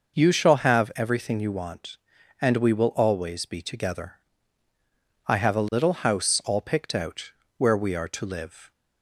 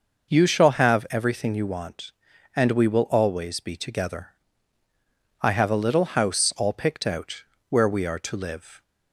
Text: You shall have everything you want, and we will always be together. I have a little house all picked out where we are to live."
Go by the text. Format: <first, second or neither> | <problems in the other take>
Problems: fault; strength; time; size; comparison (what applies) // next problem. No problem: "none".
neither | pauses between "out" and "where"; slight; the same in both